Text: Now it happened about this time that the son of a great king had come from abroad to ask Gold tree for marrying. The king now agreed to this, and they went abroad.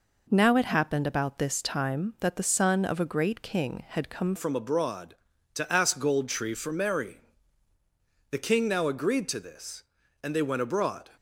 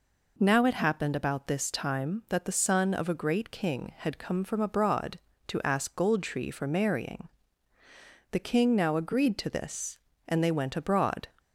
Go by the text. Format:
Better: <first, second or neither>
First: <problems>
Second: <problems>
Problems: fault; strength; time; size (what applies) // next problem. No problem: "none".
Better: second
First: changes voice at "from"; from 4.3 s on; 6.7 s long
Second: none